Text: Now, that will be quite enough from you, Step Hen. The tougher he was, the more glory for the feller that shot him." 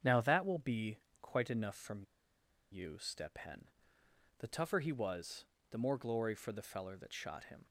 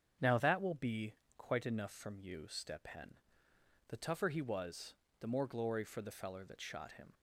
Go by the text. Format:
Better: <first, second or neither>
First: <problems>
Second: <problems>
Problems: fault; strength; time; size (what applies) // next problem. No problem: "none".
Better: second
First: starts louder than the rest; strong; until 1.2 s; 7.5 dB // pauses between "be" and "quite"; slight; at 0.9 s; 0.22 s long // pauses between "from" and "you"; noticeable; at 2.0 s; 0.68 s long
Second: starts louder than the rest; strong; until 1.4 s; 7.5 dB // pauses between "be" and "quite"; slight; at 1.1 s; 0.22 s long